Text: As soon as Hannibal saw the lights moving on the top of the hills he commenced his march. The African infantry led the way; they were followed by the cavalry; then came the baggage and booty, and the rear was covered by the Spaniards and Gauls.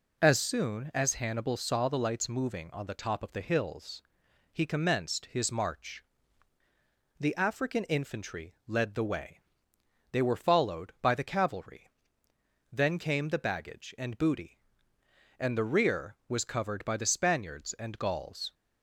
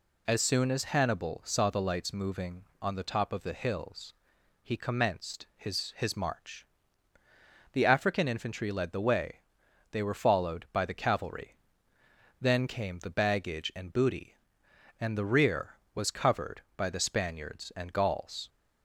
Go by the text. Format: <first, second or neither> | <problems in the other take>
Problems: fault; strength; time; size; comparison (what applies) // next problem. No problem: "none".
first | pauses between "hills" and "he"; noticeable; at 4.1 s; 0.50 s long; noticeable in the first // says "his" twice; at 5.9 s